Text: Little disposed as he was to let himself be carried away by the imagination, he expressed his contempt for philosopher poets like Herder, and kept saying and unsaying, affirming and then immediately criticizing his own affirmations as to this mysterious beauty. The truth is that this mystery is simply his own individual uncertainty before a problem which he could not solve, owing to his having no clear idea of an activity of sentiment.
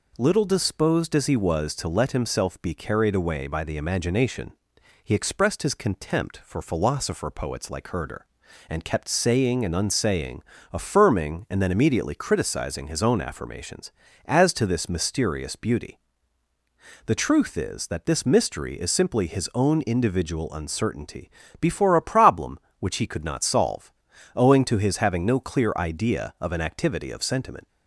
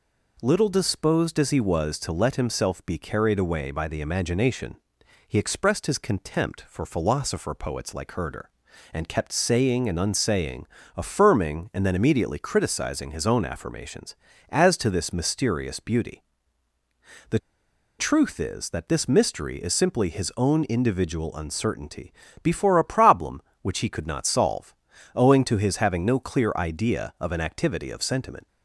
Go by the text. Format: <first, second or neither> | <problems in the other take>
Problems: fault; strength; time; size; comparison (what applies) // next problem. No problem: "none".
first | pauses between "The" and "truth"; noticeable; at 17.3 s; 0.60 s long // pauses between "uncertainty" and "before"; slight; at 22.1 s; 0.28 s long; slight in the first